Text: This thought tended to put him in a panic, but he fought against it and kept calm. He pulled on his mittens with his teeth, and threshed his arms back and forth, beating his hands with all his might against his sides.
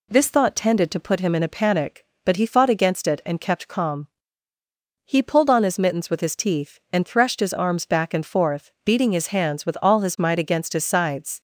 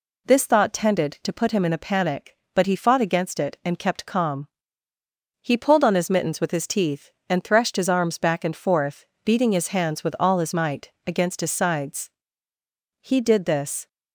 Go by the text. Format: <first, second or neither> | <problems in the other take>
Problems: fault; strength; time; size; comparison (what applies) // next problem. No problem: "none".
first | pauses between "might" and "against"; slight; at 10.8 s; 0.16 s long // goes on to say "He did this"; noticeable; from 12.9 s on; 0.88 s long